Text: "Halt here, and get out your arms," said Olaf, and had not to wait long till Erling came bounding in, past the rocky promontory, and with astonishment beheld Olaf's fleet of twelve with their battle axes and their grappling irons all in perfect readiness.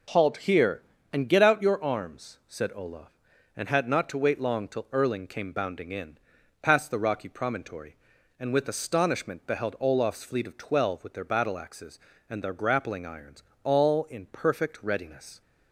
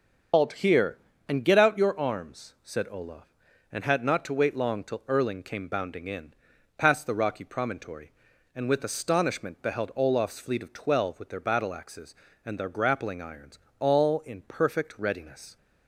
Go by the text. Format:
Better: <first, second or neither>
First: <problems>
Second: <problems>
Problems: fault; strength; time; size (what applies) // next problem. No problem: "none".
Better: first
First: pauses between "irons" and "all"; slight; at 13.4 s; 0.20 s long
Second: loses the start of "Halt"; at 0.3 s; 100 ms // starts louder than the rest; until 1.6 s; 6.5 dB // pauses between "irons" and "all"; slight; at 13.5 s; 0.20 s long